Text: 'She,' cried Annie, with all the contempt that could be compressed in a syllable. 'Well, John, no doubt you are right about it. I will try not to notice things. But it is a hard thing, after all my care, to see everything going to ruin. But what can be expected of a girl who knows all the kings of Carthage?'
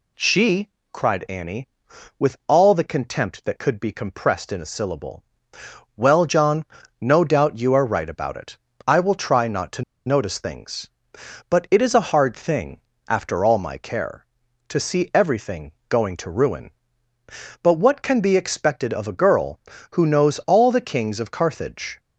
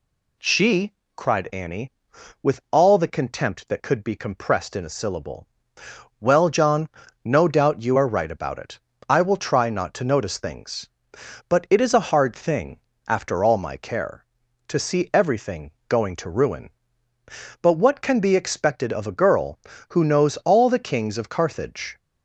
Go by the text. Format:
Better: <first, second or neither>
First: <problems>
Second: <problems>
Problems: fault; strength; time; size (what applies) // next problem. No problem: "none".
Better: second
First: pauses between "to" and "notice"; slight; at 9.8 s; 0.24 s long // pauses between "everything" and "going"; slight; at 15.7 s; 0.18 s long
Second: pauses between "everything" and "going"; slight; at 15.7 s; 0.18 s long